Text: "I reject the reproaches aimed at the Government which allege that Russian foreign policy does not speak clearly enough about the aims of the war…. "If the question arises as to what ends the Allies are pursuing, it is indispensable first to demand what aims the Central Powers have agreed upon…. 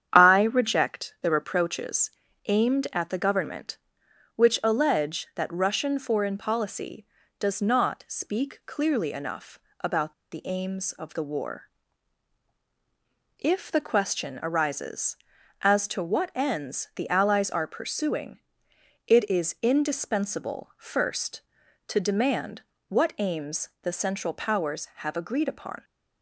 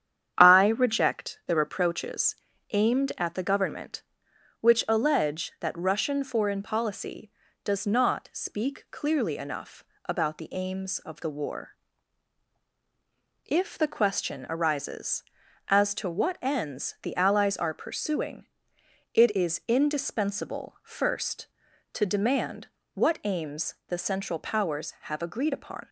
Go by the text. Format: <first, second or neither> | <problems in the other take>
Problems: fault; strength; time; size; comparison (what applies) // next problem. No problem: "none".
second | starts louder than the rest; strong; until 1.1 s; 9 dB; strong in the second // pauses between "reproaches" and "aimed"; slight; at 2.0 s; 0.36 s long; slight in the second // pauses between "enough" and "about"; slight; at 9.5 s; 0.22 s long; slight in the second // pauses between "about" and "the"; slight; at 10.1 s; 0.20 s long // pauses between "demand" and "what"; slight; at 22.6 s; 0.26 s long; slight in the second